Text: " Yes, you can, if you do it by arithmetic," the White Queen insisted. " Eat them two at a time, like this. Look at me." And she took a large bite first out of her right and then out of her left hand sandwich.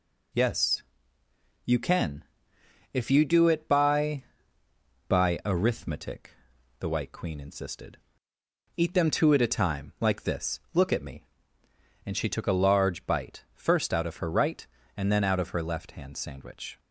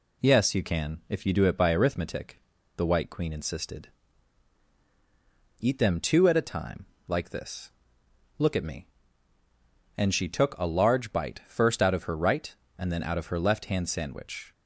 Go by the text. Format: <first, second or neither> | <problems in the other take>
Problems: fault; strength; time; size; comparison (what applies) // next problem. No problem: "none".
second | says "by" twice; at 5.0 s